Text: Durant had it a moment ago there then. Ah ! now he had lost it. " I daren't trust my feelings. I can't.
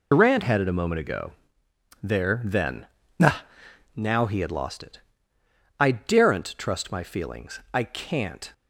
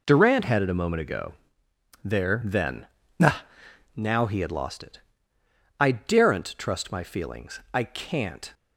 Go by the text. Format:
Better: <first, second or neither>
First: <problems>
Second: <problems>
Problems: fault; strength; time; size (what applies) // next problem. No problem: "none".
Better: second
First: loses the start of "Durant"; at 0.1 s; 70 ms // pauses between "ago" and "there"; noticeable; at 1.3 s; 0.70 s long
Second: pauses between "ago" and "there"; noticeable; at 1.3 s; 0.70 s long